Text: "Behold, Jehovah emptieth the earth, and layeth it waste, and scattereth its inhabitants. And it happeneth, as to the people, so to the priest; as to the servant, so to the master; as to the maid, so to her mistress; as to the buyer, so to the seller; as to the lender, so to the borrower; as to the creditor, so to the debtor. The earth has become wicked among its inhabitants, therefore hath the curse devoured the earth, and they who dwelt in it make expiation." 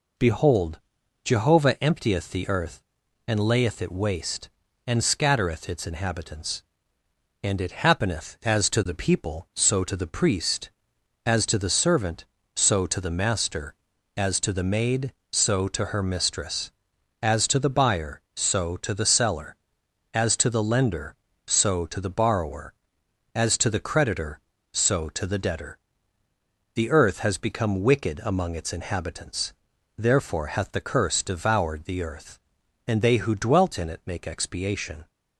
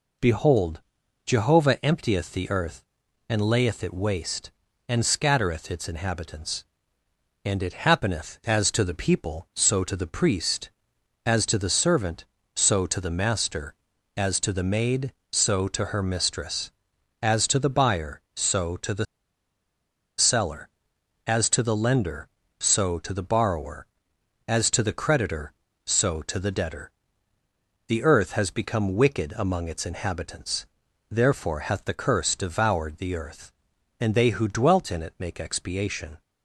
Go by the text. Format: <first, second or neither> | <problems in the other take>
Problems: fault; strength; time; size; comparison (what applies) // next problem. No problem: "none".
first | pauses between "the" and "seller"; at 19.0 s; 1.1 s long